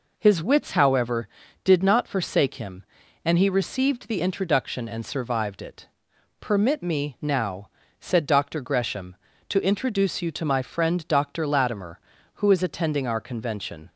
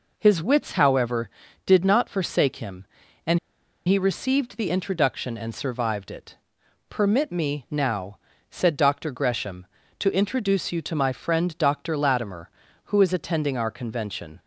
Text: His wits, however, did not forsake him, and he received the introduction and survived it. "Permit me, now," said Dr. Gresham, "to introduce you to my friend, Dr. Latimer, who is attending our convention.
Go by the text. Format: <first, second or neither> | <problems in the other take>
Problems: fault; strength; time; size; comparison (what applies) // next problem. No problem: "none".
first | pauses between "and" and "he"; noticeable; at 3.3 s; 0.48 s long